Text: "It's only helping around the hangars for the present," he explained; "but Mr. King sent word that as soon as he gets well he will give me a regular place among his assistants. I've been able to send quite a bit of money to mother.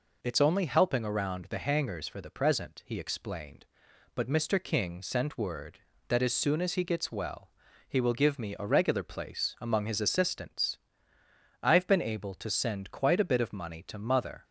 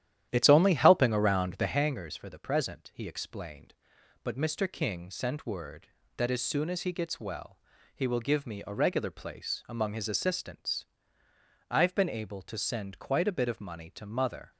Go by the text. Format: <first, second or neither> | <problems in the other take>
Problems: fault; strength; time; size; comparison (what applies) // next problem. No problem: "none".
first | starts louder than the rest; strong; until 1.9 s; 11 dB // pauses between "well" and "he"; at 7.5 s; 0.38 s long; also in the first